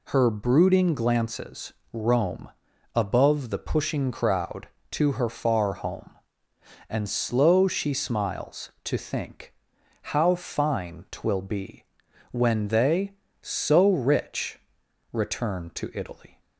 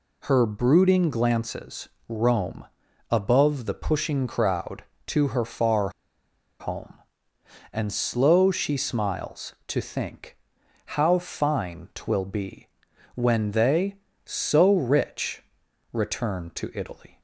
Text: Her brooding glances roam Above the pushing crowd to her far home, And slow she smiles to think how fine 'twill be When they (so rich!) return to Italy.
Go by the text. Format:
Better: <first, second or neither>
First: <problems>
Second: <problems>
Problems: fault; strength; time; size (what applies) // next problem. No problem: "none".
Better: first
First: pauses between "glances" and "roam"; slight; at 1.7 s; 0.20 s long // pauses between "roam" and "Above"; at 2.4 s; 0.44 s long // pauses between "think" and "how"; noticeable; at 9.5 s; 0.50 s long // pauses between "be" and "When"; noticeable; at 11.8 s; 0.46 s long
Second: pauses between "glances" and "roam"; slight; at 1.8 s; 0.20 s long // pauses between "roam" and "Above"; at 2.6 s; 0.44 s long // pauses between "far" and "home"; noticeable; at 5.9 s; 0.69 s long // pauses between "think" and "how"; noticeable; at 10.3 s; 0.50 s long // pauses between "be" and "When"; noticeable; at 12.6 s; 0.46 s long